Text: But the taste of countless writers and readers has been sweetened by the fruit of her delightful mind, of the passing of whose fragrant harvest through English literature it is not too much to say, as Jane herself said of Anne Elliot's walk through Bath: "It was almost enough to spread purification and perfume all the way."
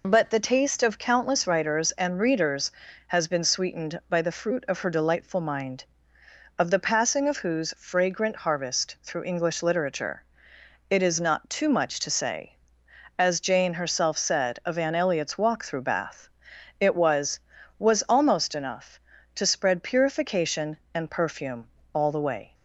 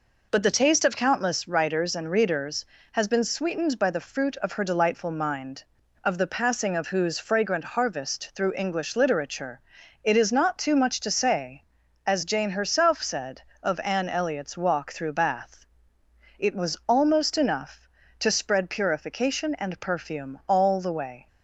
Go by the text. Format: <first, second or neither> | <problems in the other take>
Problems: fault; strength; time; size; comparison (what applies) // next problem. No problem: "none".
second | pauses between "literature" and "it"; noticeable; at 10.2 s; 0.70 s long; also in the second // says "was" twice; at 17.7 s // pauses between "perfume" and "all"; slight; at 21.6 s; 0.26 s long